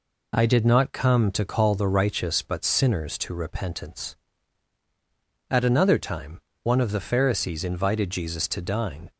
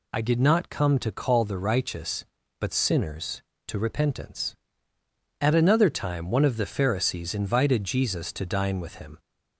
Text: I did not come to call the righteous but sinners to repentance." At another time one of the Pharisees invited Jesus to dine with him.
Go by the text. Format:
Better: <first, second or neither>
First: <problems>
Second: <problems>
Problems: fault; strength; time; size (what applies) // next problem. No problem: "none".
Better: second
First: pauses between "time" and "one"; slight; at 6.4 s; 0.24 s long // stops before "with him"; at 9.1 s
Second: none